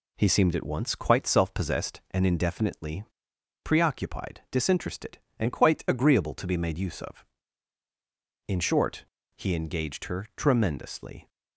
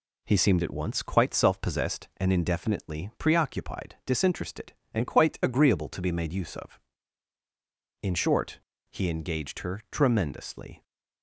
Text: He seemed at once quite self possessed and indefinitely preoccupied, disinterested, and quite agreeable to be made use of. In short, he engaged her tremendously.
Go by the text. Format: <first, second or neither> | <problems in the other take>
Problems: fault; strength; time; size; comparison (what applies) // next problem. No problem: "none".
second | pauses between "indefinitely" and "preoccupied"; noticeable; at 3.0 s; 0.61 s long